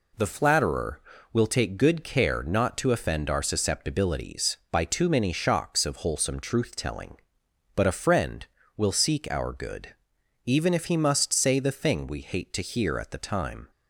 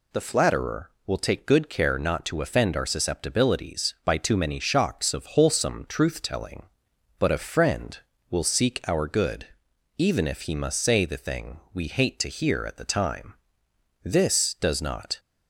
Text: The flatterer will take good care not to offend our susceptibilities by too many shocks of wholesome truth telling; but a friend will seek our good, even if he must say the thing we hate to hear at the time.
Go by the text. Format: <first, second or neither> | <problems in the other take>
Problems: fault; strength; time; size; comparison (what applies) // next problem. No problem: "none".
first | pauses between "thing" and "we"; slight; at 11.5 s; 0.16 s long // goes on to say "This does not"; noticeable; from 14.0 s on; 1.1 s long